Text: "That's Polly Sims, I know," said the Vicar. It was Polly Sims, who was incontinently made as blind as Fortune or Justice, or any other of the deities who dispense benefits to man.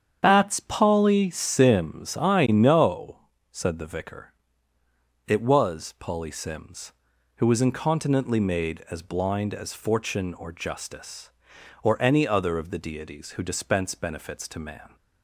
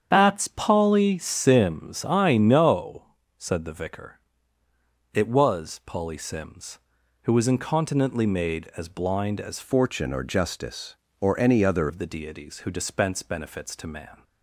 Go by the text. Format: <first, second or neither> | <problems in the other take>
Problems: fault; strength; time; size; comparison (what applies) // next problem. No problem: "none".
first | starts louder than the rest; strong; until 1.1 s; 8 dB; strong in the first // changes voice from "Fortune" to "other"; from 9.6 to 11.9 s; 2.3 s long